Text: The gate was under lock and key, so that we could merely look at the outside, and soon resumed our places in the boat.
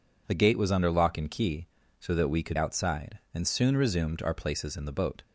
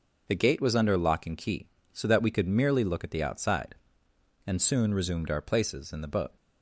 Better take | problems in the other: second | skips "merely look at the"; at 2.5 s

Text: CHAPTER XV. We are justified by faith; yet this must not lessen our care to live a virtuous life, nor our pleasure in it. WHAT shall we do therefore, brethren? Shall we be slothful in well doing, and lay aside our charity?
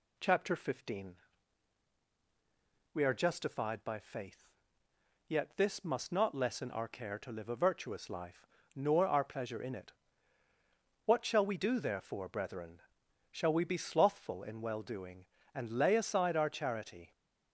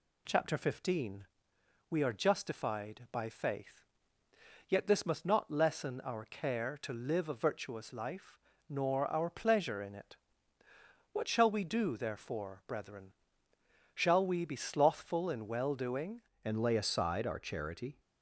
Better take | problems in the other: first | changes voice at "and"; from 16.4 s on; 1.5 s long

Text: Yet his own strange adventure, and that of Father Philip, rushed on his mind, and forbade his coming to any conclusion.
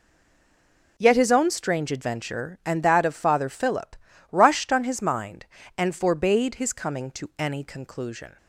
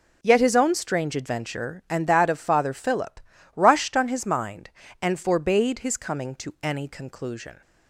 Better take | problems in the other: second | stays silent before the first word; until 0.9 s; 0.9 s long

